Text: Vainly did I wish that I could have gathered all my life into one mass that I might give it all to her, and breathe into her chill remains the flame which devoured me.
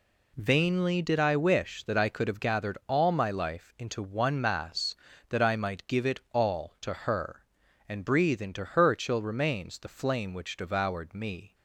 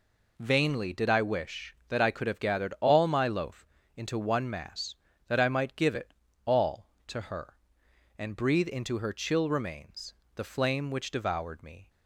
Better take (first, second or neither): first